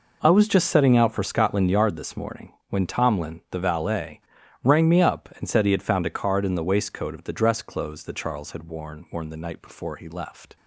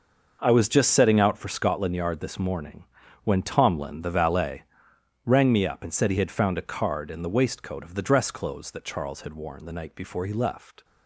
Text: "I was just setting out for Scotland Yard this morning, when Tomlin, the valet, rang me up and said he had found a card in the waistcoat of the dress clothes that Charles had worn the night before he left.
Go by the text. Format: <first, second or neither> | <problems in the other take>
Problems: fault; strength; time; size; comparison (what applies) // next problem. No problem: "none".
second | says "worn" twice; at 9.1 s